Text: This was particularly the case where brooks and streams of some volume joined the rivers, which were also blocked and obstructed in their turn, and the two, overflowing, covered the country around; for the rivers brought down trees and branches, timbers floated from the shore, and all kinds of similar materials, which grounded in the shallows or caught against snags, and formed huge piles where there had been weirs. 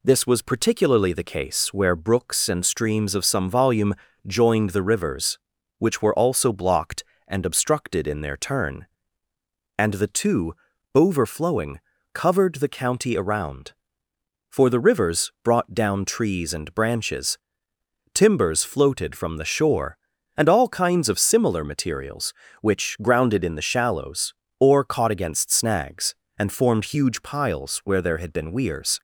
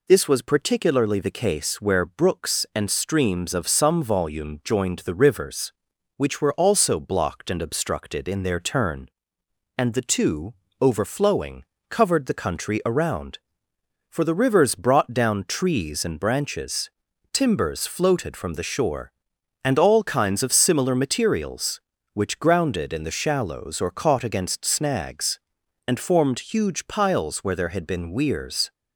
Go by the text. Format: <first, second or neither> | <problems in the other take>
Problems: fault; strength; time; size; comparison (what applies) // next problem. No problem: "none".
second | pauses between "volume" and "joined"; slight; at 3.9 s; 0.32 s long // says "county" for "country"; at 12.6 s